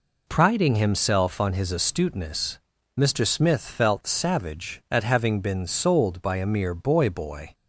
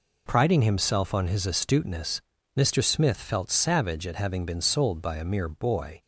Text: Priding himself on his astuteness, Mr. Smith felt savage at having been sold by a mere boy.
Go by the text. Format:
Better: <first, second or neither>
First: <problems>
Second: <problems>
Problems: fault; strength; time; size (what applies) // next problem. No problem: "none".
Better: second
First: says "boy" twice; at 7.0 s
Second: none